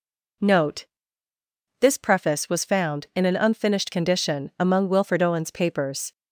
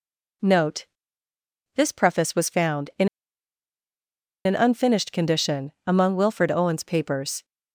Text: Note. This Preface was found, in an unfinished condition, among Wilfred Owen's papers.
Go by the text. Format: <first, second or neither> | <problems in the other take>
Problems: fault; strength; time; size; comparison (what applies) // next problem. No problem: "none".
first | pauses between "in" and "an"; strong; at 3.0 s; 1.3 s long